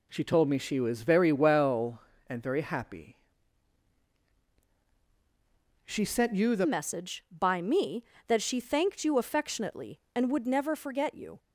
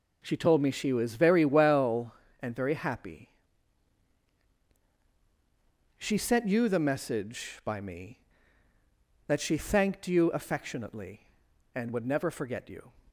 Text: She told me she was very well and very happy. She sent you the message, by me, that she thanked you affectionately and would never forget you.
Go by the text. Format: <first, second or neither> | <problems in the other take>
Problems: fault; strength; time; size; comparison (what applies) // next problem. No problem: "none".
second | changes voice at "message"; from 6.6 s on; 4.7 s long